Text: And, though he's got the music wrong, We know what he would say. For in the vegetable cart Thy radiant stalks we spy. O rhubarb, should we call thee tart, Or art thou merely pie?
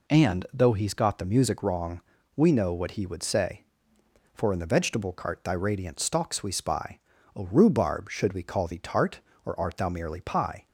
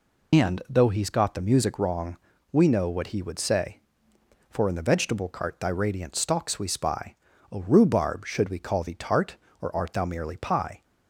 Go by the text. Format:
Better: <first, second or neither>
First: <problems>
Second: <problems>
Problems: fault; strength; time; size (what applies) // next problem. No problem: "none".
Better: first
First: none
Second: loses the start of "And"; at 0.3 s; 80 ms